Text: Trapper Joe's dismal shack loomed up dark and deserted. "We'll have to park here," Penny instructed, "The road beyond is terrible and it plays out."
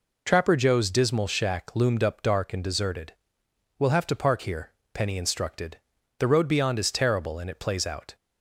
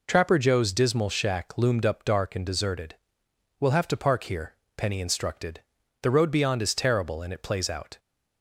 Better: neither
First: none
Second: none

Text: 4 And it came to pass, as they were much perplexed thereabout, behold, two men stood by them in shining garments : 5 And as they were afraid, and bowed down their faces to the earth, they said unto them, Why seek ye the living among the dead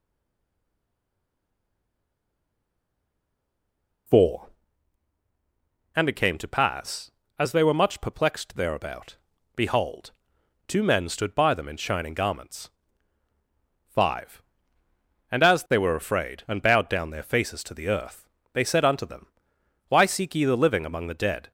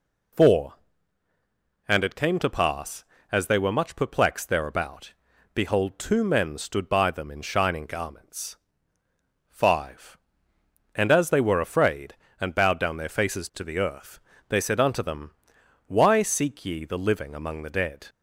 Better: second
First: stays silent before the first word; strong; until 4.0 s; 4.0 s long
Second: none

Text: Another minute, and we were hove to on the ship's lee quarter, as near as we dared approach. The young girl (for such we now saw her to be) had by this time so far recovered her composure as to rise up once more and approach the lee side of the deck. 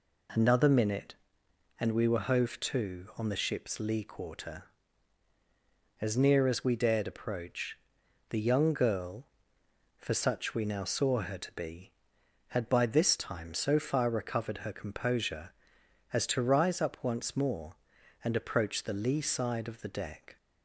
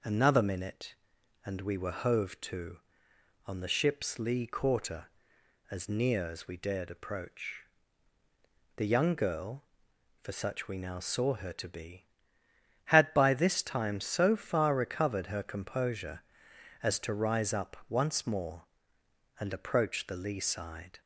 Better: first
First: none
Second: stops before "of the deck"; at 21.0 s

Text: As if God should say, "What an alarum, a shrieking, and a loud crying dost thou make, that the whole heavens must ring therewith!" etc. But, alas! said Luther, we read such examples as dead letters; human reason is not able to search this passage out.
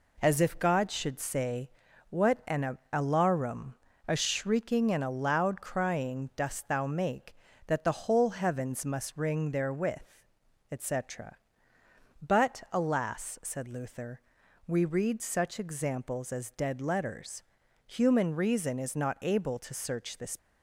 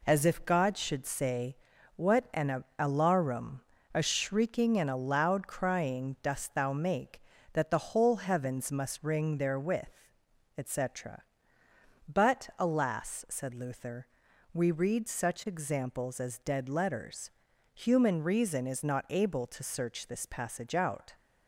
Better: second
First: stops before "passage out"; at 20.3 s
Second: none

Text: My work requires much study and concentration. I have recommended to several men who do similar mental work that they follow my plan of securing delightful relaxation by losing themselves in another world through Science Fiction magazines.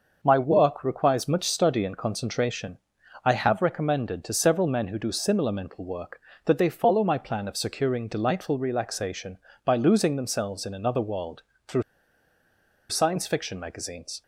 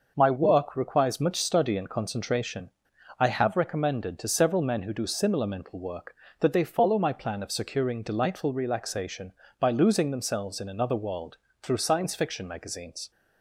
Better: second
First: starts louder than the rest; noticeable; until 1.2 s; 6 dB // pauses between "world" and "through"; slight; at 11.4 s; 0.26 s long // pauses between "through" and "Science"; at 11.8 s; 1.0 s long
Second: starts louder than the rest; noticeable; until 1.1 s; 6 dB // pauses between "world" and "through"; slight; at 11.3 s; 0.26 s long

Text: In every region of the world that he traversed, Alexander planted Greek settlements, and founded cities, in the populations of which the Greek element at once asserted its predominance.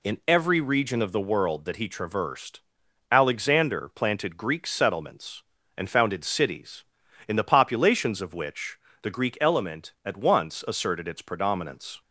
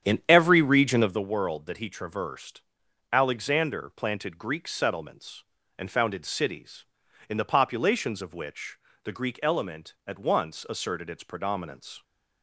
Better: first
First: pauses between "which" and "the"; slight; at 8.7 s; 0.24 s long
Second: starts louder than the rest; strong; until 1.2 s; 9 dB // pauses between "which" and "the"; slight; at 8.7 s; 0.26 s long

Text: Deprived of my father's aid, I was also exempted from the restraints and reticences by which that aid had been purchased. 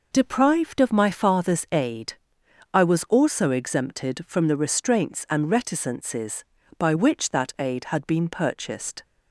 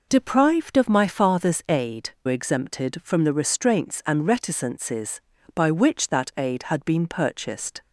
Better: first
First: none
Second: skips "I was also"; at 2.1 s

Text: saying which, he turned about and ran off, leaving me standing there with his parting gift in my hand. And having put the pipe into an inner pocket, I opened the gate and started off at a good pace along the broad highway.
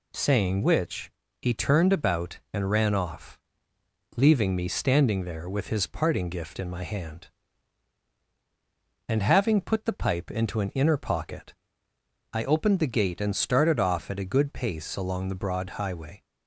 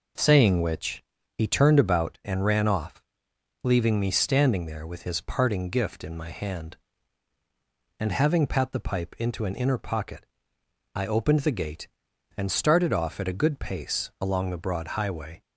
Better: first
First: none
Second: says "pat" for "put"; at 8.4 s

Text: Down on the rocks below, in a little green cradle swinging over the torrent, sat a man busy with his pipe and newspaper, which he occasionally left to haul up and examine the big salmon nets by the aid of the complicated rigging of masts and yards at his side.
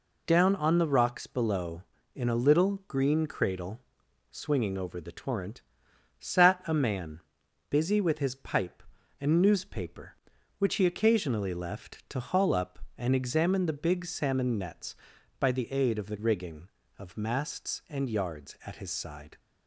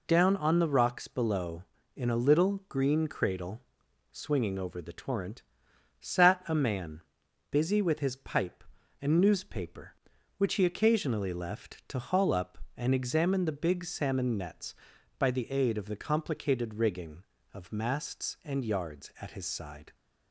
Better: second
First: pauses between "cradle" and "swinging"; noticeable; at 3.7 s; 0.52 s long // pauses between "man" and "busy"; noticeable; at 7.1 s; 0.50 s long // skips "complicated"; at 16.1 s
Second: pauses between "cradle" and "swinging"; noticeable; at 3.6 s; 0.52 s long // pauses between "man" and "busy"; noticeable; at 7.0 s; 0.50 s long

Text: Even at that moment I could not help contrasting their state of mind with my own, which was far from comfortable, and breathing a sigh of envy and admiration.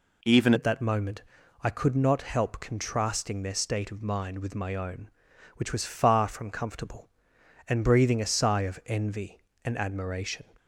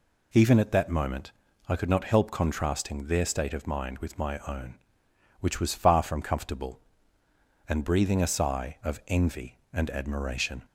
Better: second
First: changes voice at "at"; from 0.5 s on; 9.9 s long // pauses between "moment" and "I"; at 1.2 s; 0.40 s long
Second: pauses between "moment" and "I"; slight; at 1.3 s; 0.36 s long

